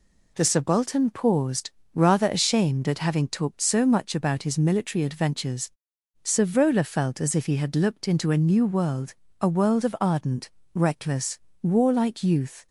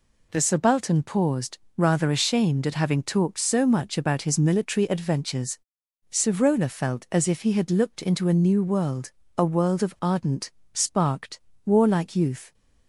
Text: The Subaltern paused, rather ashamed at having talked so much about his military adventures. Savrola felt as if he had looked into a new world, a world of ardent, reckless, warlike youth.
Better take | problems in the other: first | says "sparked" for "reckless"; at 10.7 s

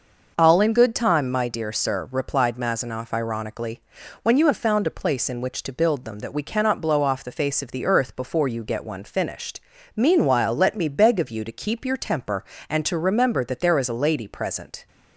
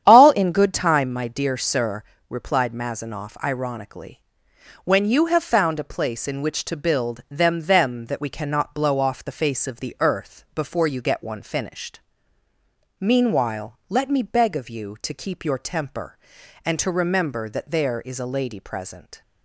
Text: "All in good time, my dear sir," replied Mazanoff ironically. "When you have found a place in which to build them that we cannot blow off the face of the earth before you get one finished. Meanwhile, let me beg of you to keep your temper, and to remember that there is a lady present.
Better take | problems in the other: first | starts louder than the rest; strong; until 1.0 s; 9.5 dB; noticeable in the first // says "them" twice; at 7.6 s

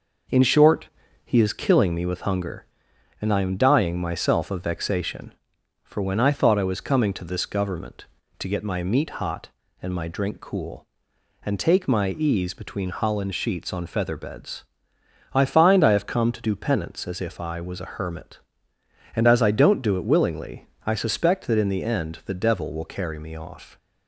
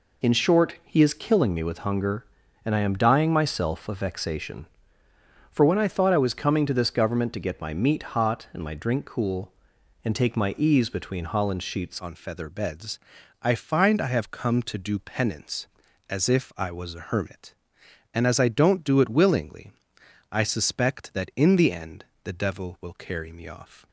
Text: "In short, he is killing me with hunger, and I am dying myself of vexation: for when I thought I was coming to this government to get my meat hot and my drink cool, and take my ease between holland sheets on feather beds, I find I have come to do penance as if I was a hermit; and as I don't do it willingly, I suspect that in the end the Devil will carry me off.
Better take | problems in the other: first | changes voice at "on"; from 11.9 s on; 11.9 s long // pauses between "end" and "the"; slight; at 22.0 s; 0.18 s long

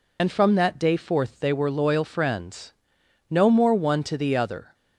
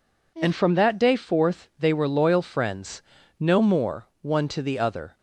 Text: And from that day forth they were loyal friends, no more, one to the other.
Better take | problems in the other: second | loses the start of "And"; at 0.1 s; 45 ms

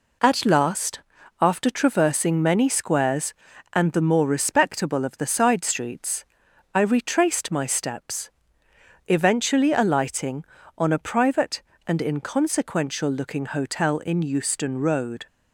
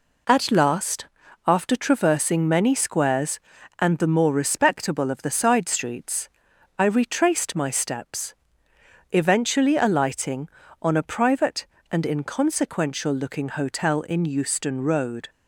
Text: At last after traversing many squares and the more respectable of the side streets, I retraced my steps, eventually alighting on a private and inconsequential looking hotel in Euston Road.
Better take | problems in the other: neither | pauses between "last" and "after"; the same in both

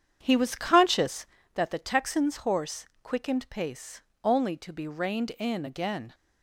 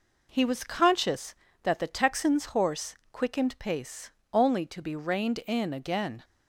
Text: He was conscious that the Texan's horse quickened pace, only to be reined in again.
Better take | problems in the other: second | starts louder than the rest; strong; until 1.5 s; 8.5 dB // pauses between "horse" and "quickened"; slight; at 2.8 s; 0.18 s long; slight in the second

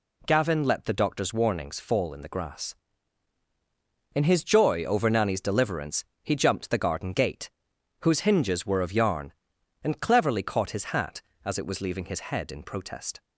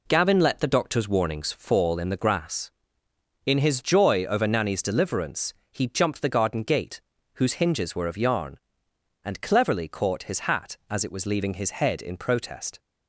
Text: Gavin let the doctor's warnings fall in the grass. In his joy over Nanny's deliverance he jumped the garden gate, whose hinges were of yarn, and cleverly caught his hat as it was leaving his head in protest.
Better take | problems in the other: neither | pauses between "deliverance" and "he"; slight; the same in both

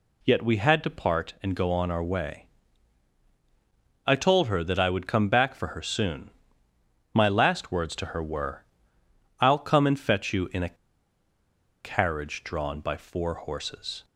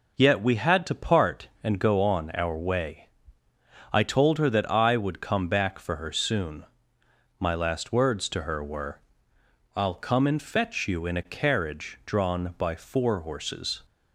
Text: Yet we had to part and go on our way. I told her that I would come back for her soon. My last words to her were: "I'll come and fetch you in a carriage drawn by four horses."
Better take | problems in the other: second | pauses between "a" and "carriage"; at 10.7 s; 1.0 s long

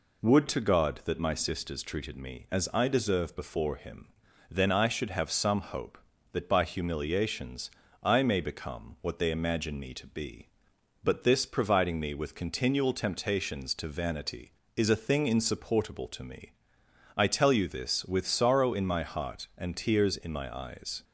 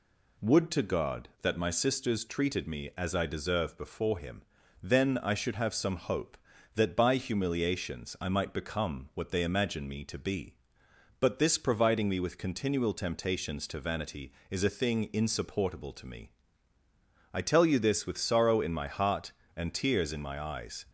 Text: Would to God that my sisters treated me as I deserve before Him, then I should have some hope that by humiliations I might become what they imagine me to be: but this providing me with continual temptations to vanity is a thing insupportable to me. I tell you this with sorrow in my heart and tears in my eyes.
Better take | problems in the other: second | pauses between "humiliations" and "I"; slight; at 7.6 s; 0.34 s long // says "may" for "might"; at 8.2 s

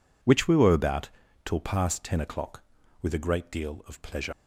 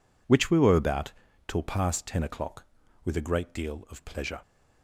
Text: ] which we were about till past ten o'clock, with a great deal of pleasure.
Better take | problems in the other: second | pauses between "about" and "till"; slight; at 1.0 s; 0.36 s long; slight in the second // leaves "pleasure" unfinished; at 4.3 s; 60 ms

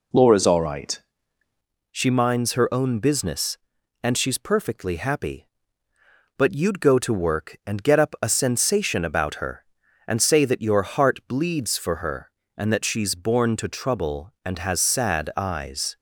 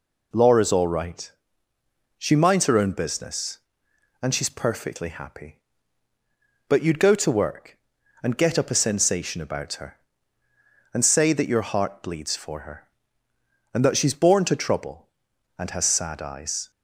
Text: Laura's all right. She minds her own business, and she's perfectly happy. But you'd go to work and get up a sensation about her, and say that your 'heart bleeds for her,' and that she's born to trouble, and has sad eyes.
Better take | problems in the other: second | changes voice at "She"; from 1.9 s on; 14.0 s long

